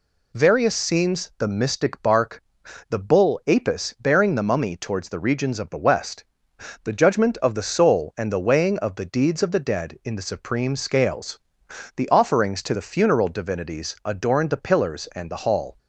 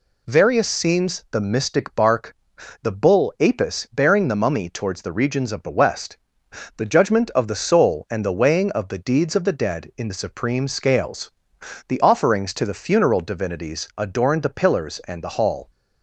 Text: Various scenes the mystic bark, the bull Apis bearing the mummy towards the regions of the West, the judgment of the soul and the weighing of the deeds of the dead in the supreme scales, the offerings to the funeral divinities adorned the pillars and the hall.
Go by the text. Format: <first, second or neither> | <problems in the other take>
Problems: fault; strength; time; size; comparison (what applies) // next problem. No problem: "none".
neither | none